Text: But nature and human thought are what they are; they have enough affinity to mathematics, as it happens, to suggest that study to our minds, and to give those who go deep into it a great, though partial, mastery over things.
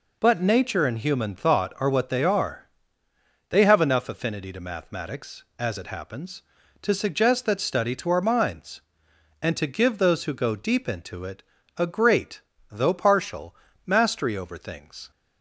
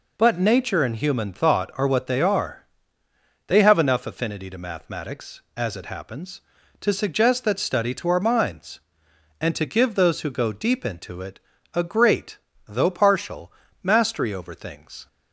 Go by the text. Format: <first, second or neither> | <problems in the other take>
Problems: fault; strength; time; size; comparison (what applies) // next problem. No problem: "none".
neither | pauses between "it" and "a"; slight; the same in both